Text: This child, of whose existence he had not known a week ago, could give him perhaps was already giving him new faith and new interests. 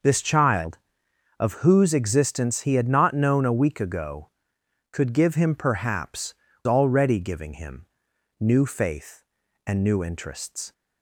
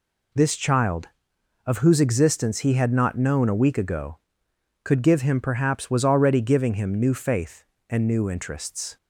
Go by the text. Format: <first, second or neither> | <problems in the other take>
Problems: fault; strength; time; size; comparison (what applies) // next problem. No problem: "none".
second | skips "was"; at 6.5 s // pauses between "him" and "new"; noticeable; at 7.8 s; 0.54 s long